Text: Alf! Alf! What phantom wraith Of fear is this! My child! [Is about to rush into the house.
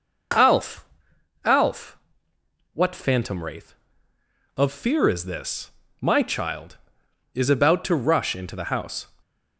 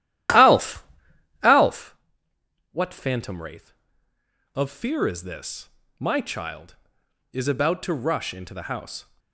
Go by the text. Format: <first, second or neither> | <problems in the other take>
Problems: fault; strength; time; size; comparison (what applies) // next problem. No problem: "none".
first | starts louder than the rest; strong; until 2.0 s; 12.5 dB